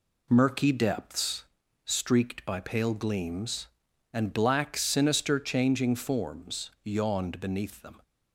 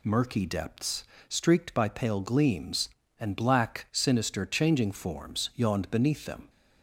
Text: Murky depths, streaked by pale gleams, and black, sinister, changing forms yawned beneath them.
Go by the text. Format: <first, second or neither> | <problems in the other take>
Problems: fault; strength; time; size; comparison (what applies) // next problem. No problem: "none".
neither | none